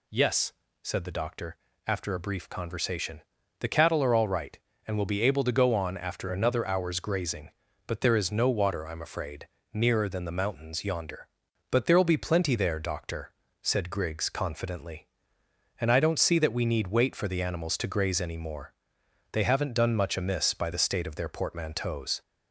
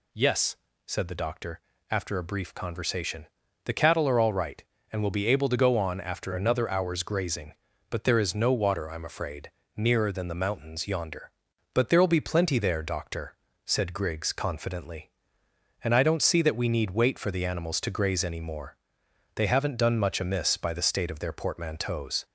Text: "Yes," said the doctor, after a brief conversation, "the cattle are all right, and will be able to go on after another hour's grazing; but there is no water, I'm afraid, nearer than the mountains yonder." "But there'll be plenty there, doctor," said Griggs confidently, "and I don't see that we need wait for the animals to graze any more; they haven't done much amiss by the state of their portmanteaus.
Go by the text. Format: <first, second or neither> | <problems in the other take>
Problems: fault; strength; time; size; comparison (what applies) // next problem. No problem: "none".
neither | none